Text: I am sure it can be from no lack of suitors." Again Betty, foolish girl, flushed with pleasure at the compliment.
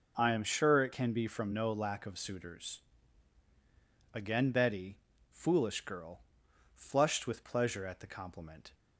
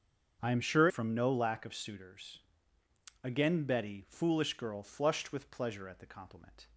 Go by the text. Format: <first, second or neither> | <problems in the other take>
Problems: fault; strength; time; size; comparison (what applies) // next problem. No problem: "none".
first | starts louder than the rest; until 1.4 s; 7 dB // skips "it can be"; at 0.8 s